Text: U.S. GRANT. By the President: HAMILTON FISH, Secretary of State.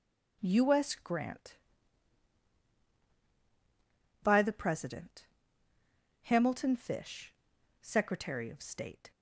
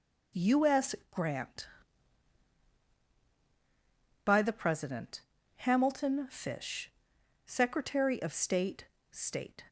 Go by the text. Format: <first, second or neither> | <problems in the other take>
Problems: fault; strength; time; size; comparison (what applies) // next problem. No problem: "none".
first | says "State" twice; at 9.1 s